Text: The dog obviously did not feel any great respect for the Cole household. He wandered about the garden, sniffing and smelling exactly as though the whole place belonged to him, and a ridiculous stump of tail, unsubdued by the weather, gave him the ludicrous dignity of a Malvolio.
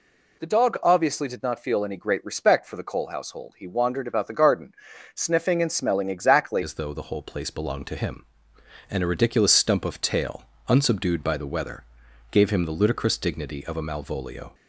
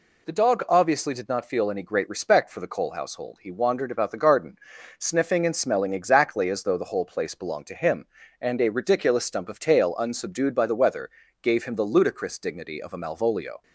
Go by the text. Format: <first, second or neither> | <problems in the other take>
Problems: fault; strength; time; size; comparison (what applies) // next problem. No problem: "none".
second | changes voice at "as"; from 6.6 s on; 7.9 s long